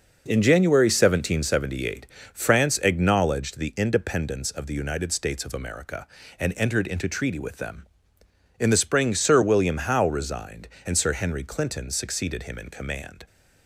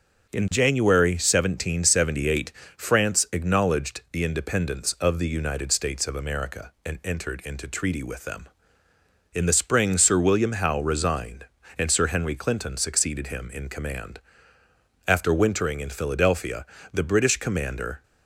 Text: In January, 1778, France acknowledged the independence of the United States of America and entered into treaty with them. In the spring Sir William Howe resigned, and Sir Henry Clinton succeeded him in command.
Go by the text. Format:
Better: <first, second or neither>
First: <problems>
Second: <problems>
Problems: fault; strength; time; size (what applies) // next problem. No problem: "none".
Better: first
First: none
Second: starts louder than the rest; noticeable; until 1.3 s; 6 dB // goes on to say "After wintering in Philadelphia the British commander"; strong; from 15.0 s on; 2.9 s long